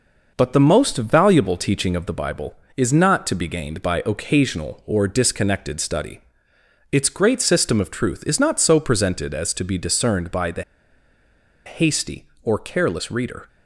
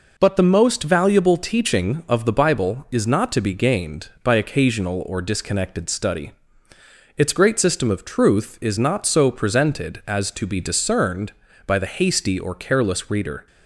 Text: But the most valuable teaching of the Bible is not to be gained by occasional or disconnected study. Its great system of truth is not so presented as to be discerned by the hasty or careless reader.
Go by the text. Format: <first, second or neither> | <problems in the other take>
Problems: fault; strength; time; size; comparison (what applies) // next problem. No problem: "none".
second | pauses between "the" and "hasty"; at 10.6 s; 1.0 s long